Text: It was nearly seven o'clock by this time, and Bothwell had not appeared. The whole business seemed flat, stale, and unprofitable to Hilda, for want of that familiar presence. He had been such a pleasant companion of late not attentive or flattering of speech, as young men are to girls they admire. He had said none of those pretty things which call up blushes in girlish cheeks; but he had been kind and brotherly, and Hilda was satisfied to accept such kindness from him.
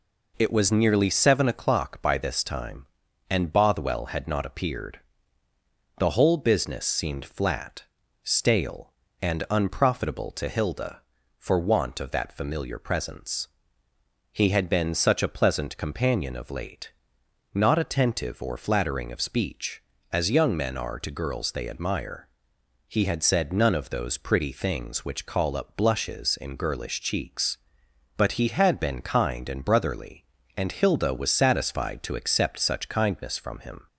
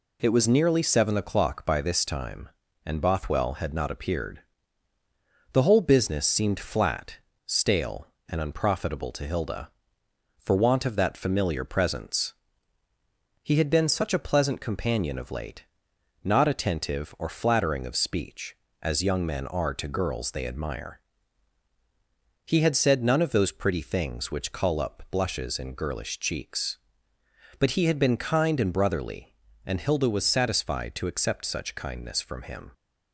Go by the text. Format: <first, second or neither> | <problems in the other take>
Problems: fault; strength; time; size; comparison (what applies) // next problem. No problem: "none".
neither | pauses between "late" and "not"; noticeable; the same in both